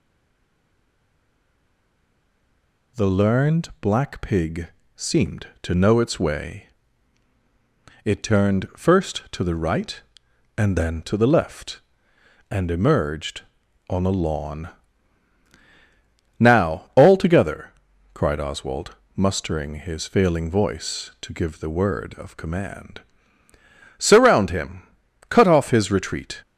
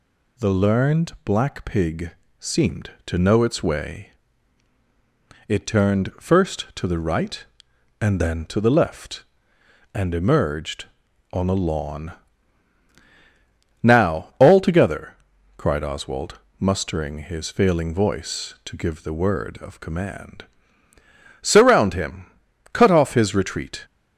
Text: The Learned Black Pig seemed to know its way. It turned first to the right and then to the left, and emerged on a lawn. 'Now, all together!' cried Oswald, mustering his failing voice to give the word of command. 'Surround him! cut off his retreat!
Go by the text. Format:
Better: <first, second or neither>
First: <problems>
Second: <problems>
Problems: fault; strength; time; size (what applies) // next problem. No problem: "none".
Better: second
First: stays silent before the first word; strong; until 2.9 s; 2.9 s long // pauses between "Pig" and "seemed"; slight; at 4.6 s; 0.28 s long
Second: pauses between "Pig" and "seemed"; slight; at 2.1 s; 0.28 s long